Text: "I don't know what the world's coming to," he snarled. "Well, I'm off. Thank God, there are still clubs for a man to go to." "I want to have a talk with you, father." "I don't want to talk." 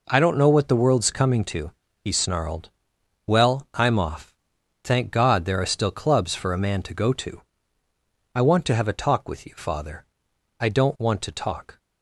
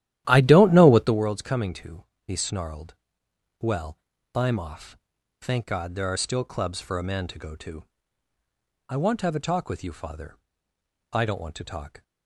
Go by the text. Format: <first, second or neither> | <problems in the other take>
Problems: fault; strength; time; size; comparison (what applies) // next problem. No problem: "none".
first | starts louder than the rest; strong; until 1.2 s; 12.5 dB